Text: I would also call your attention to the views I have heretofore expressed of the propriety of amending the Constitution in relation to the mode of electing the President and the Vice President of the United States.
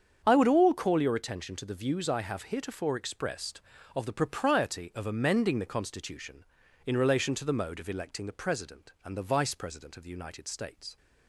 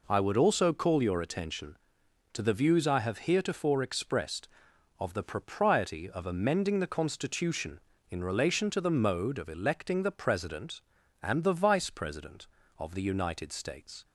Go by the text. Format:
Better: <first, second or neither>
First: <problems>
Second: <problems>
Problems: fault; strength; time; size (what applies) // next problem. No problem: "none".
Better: second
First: starts louder than the rest; strong; until 1.2 s; 7.5 dB // says "all" for "also"; at 0.4 s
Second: none